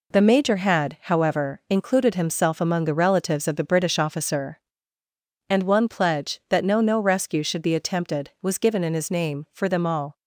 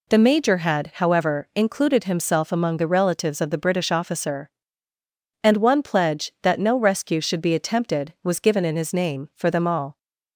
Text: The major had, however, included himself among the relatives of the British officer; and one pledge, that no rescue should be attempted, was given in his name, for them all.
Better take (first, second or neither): second